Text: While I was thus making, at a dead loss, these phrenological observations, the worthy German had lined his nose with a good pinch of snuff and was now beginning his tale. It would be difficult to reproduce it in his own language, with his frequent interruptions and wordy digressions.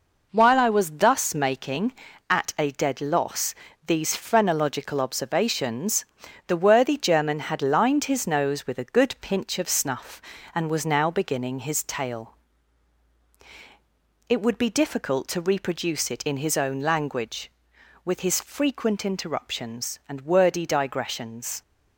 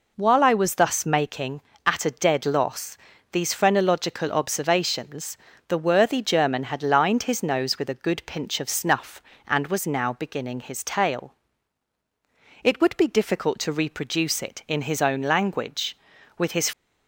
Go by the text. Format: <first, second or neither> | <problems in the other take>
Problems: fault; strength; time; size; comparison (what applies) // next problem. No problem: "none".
first | stops before "frequent interruptions and wordy digressions"; at 16.7 s